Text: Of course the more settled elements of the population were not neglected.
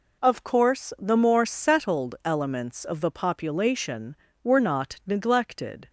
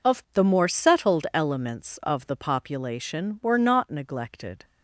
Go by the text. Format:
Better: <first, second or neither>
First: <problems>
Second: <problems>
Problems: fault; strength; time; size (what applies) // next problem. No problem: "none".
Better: first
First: none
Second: skips "course"; at 0.2 s